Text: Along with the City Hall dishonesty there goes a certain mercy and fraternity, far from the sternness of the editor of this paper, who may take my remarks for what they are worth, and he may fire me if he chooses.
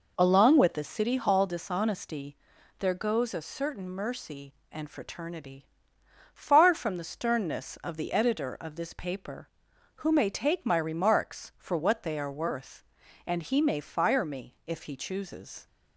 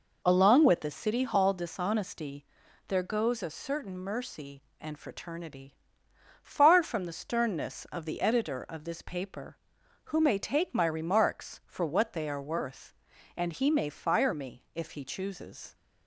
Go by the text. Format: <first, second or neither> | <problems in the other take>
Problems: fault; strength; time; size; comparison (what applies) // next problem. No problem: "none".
neither | pauses between "dishonesty" and "there"; the same in both